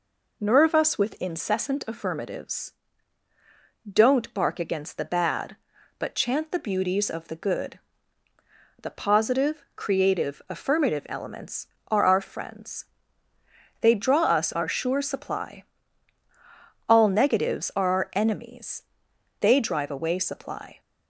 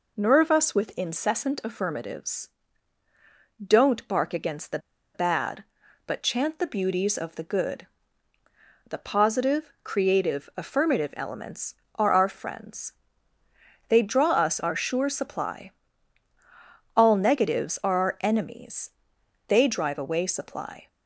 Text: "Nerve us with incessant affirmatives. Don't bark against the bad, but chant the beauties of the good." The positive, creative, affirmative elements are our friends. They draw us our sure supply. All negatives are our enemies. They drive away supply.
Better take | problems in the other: first | pauses between "the" and "bad"; at 4.7 s; 0.36 s long

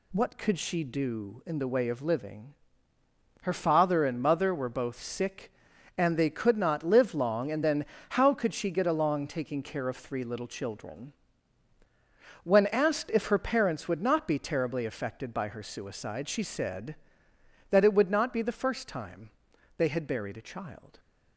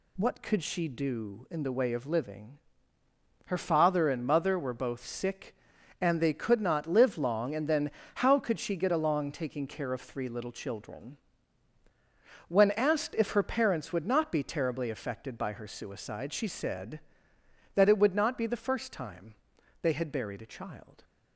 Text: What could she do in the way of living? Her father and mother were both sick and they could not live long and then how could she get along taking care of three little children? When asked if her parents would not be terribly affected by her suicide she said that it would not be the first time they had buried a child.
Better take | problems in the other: neither | pauses between "then" and "how"; slight; the same in both // pauses between "time" and "they"; noticeable; the same in both

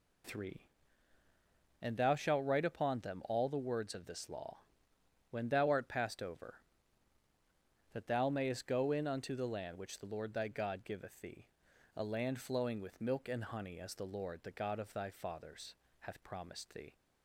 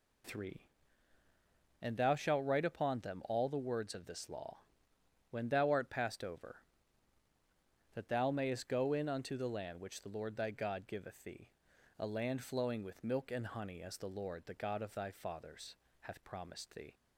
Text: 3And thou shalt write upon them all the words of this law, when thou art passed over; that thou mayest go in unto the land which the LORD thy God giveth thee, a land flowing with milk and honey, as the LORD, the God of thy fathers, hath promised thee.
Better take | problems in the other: neither | none

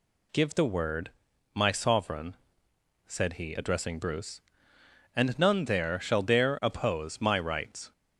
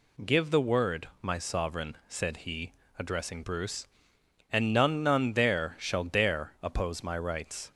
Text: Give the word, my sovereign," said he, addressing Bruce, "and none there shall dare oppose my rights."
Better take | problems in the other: first | says "none" twice; at 5.0 s

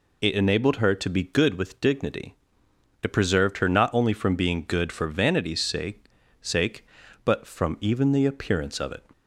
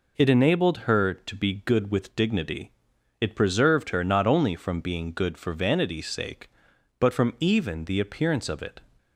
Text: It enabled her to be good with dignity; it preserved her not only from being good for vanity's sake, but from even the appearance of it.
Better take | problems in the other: second | says "sake" twice; at 6.4 s

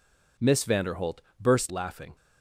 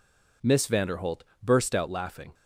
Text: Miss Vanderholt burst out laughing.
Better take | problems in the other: second | pauses between "Vanderholt" and "burst"; slight; at 1.2 s; 0.20 s long; slight in the second // skips "out"; at 1.7 s

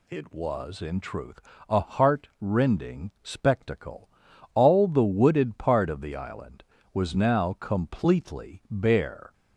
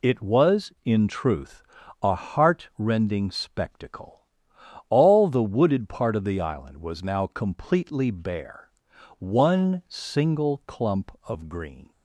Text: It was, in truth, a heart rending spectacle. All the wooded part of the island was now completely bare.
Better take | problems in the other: first | goes on to say "One single clump of green"; strong; from 9.1 s on; 2.7 s long

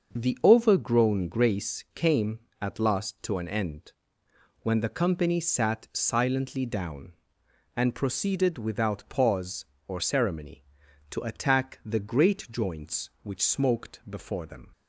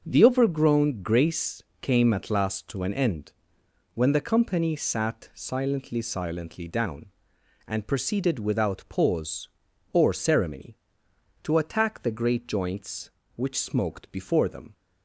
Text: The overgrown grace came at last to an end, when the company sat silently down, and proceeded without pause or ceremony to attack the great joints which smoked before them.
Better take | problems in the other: first | starts louder than the rest; until 1.0 s; 6.5 dB; also in the first // pauses between "grace" and "came"; slight; at 1.6 s; 0.18 s long // says "silently" twice; at 6.0 s

